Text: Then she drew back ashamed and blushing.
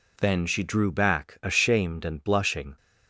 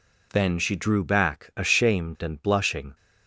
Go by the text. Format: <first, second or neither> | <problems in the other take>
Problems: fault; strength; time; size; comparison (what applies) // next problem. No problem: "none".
neither | none